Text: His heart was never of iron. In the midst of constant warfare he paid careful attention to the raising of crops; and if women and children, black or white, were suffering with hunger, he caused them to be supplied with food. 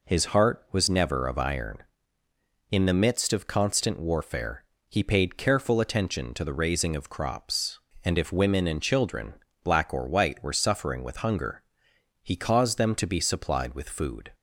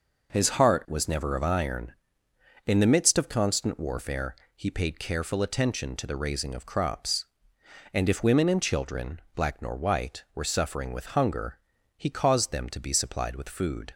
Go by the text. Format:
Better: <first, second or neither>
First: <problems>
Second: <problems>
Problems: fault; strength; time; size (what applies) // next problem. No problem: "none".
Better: first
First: pauses between "warfare" and "he"; slight; at 4.6 s; 0.24 s long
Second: pauses between "warfare" and "he"; slight; at 4.3 s; 0.20 s long // says "nor" for "or"; at 9.6 s